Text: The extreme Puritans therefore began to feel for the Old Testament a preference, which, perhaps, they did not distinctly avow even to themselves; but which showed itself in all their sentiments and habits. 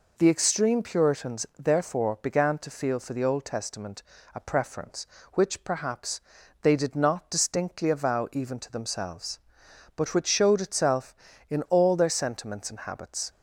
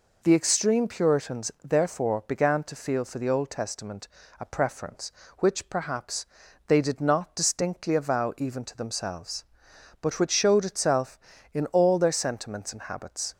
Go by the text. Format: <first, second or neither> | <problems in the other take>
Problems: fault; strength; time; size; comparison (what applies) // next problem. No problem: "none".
neither | pauses between "Testament" and "a"; slight; the same in both